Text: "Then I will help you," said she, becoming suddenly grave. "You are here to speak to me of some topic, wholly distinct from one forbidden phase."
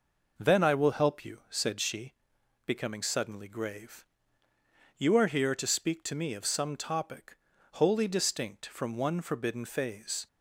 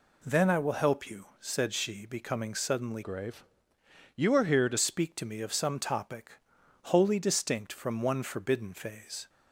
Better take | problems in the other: first | changes voice from "grave" to "to"; from 3.0 to 4.7 s; 1.7 s long

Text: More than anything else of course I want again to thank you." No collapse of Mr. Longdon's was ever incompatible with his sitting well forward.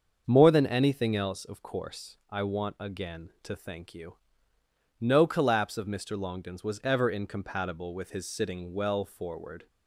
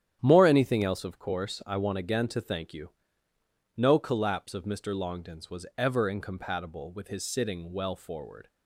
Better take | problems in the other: first | starts louder than the rest; strong; until 1.2 s; 10 dB; also in the first // skips "than"; at 0.4 s

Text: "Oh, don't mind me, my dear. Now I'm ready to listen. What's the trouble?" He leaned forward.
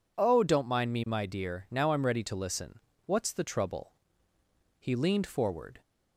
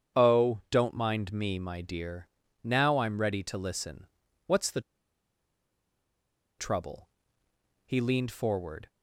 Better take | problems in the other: first | starts louder than the rest; strong; until 1.2 s; 8 dB // pauses between "the" and "trouble"; strong; at 4.8 s; 1.7 s long

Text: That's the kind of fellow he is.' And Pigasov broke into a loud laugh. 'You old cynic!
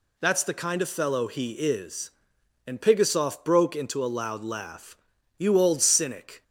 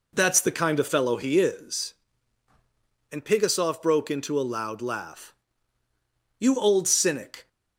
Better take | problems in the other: neither | none

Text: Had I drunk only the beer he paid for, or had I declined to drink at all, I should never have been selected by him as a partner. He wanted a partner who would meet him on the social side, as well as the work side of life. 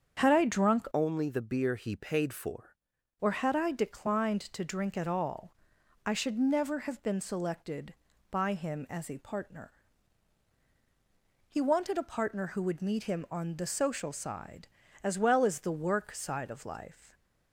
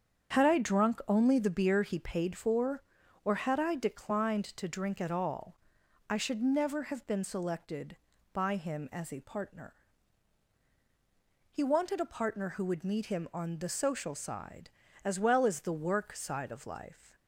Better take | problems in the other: second | starts louder than the rest; strong; until 1.2 s; 7.5 dB; strong in the second // changes voice from "only" to "for"; from 0.9 to 2.7 s; 1.8 s long

